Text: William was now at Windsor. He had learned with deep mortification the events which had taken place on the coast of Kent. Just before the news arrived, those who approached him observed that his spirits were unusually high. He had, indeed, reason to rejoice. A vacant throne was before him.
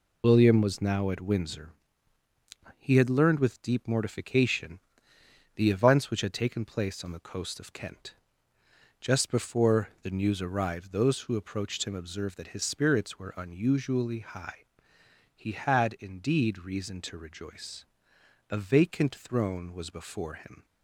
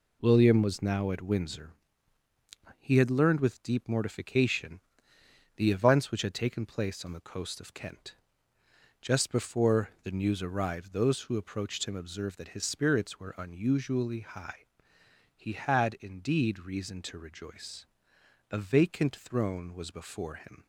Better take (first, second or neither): second